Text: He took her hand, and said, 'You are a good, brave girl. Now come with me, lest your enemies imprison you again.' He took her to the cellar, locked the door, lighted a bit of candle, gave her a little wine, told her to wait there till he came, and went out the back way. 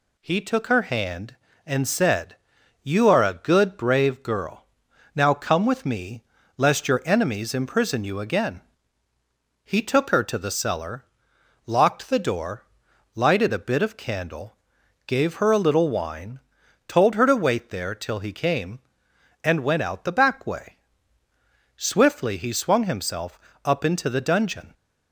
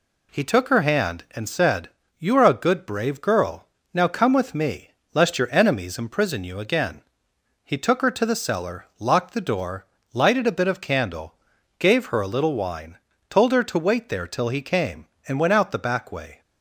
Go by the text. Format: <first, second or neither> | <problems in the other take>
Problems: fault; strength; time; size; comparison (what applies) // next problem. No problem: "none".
second | goes on to say "Swiftly he swung himself up into the dungeon"; strong; from 21.7 s on; 2.9 s long